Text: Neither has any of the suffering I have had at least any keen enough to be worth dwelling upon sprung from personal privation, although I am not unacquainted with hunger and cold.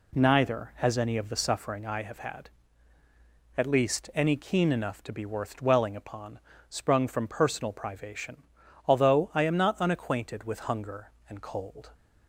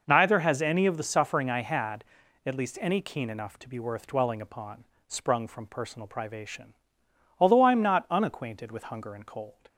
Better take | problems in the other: first | skips "have"; at 1.6 s // pauses between "upon" and "sprung"; slight; at 4.8 s; 0.22 s long; slight in the first

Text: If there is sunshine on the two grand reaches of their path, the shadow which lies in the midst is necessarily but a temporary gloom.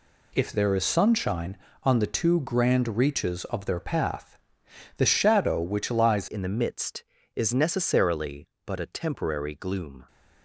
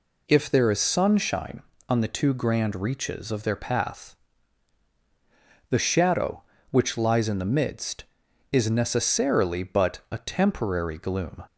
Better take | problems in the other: second | changes voice at "in"; from 6.2 s on; 3.8 s long

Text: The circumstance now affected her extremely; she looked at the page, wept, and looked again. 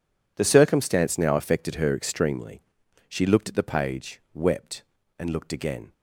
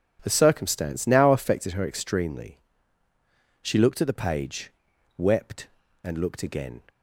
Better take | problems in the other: neither | none

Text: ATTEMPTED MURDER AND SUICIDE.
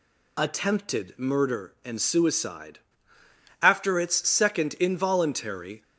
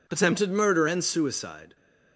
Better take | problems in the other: second | goes on to say "After its second involuntary"; strong; from 3.6 s on; 2.2 s long

